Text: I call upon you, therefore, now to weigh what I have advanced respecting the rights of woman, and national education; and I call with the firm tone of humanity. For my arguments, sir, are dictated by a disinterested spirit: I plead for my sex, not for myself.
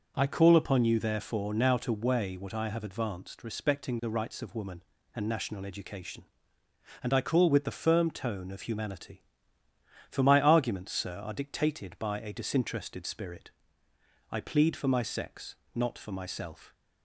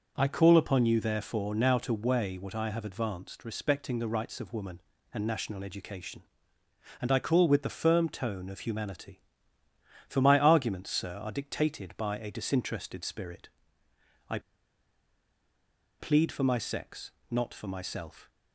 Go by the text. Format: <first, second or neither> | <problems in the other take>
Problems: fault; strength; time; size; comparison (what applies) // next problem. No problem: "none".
first | pauses between "I" and "plead"; strong; at 14.3 s; 1.6 s long